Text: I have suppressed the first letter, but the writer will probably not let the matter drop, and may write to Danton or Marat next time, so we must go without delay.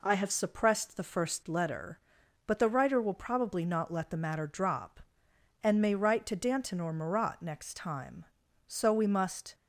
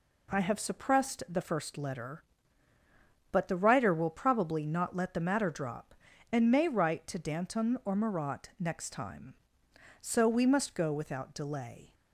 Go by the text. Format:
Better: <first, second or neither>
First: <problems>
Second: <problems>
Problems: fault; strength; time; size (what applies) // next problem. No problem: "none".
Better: second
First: stops before "go without delay"; at 9.5 s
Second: none